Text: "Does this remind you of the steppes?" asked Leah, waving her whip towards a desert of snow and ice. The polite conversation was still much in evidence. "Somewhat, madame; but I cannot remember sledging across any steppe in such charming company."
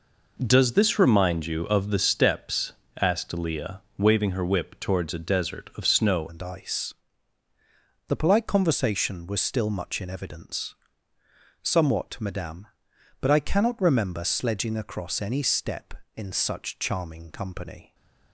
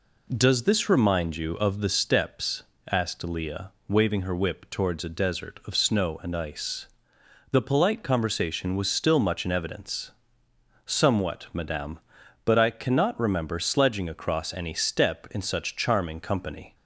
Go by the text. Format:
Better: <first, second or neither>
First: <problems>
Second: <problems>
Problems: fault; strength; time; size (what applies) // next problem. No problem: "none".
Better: second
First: changes voice at "and"; from 6.2 s on; 11.7 s long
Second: none